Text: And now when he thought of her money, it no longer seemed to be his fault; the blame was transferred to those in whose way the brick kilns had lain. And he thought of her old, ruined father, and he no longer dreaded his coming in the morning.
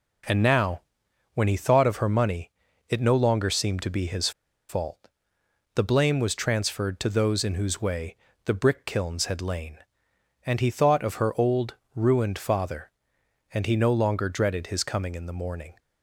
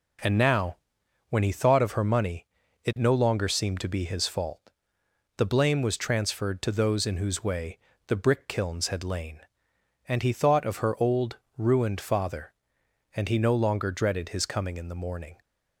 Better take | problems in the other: second | pauses between "now" and "when"; noticeable; at 0.8 s; 0.54 s long; noticeable in the second // pauses between "his" and "fault"; at 4.3 s; 0.38 s long // pauses between "way" and "the"; slight; at 8.1 s; 0.30 s long; slight in the second

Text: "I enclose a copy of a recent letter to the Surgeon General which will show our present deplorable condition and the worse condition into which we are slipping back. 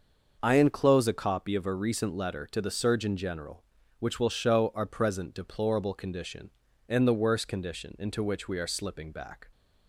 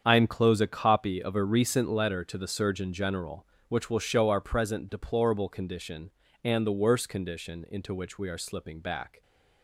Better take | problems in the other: neither | starts louder than the rest; the same in both

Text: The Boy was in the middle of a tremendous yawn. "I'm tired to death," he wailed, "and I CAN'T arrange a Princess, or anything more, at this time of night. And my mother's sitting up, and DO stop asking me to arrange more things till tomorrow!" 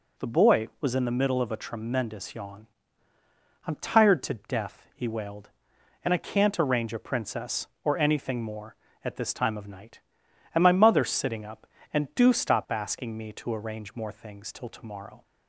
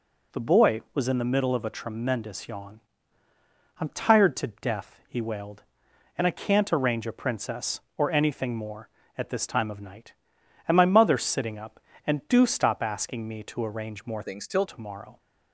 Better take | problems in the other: first | changes voice from "things" to "till"; from 14.2 to 14.6 s; 0.4 s long

